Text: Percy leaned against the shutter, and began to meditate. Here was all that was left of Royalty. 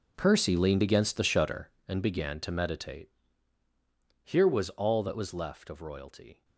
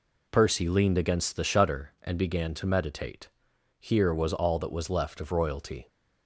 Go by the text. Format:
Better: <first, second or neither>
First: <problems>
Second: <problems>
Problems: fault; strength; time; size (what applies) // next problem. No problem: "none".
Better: second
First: gets quieter; strong; throughout; 16.5 dB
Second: none